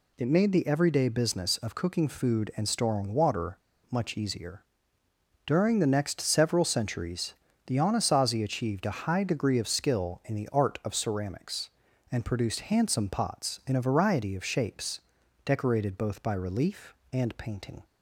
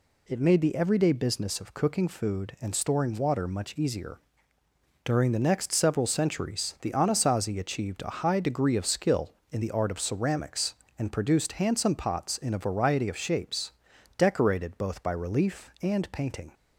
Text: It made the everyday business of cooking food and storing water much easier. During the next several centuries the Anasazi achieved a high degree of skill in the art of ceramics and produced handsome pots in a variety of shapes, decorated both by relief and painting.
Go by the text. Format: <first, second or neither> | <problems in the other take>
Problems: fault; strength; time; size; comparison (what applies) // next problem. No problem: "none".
second | pauses between "water" and "much"; slight; at 3.5 s; 0.31 s long // pauses between "centuries" and "the"; slight; at 7.3 s; 0.32 s long